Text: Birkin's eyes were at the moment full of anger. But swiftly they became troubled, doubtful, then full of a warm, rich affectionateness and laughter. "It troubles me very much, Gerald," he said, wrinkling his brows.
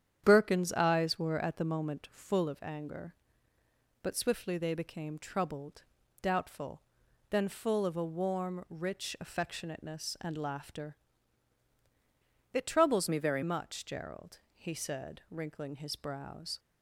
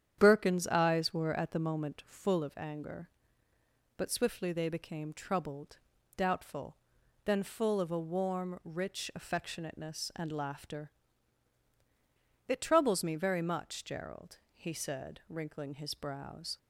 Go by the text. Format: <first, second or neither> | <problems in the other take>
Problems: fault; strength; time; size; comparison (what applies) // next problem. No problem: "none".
second | starts louder than the rest; strong; until 1.2 s; 9 dB; strong in the second // changes voice from "me" to "very"; from 13.0 to 13.4 s; 0.4 s long